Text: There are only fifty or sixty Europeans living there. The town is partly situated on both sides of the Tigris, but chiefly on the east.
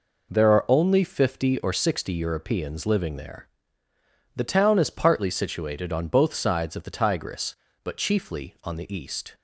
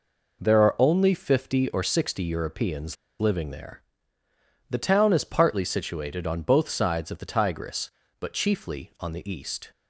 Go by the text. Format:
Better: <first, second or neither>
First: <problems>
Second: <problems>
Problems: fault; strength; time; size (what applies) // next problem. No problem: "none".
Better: first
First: none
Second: pauses between "Europeans" and "living"; slight; at 2.9 s; 0.24 s long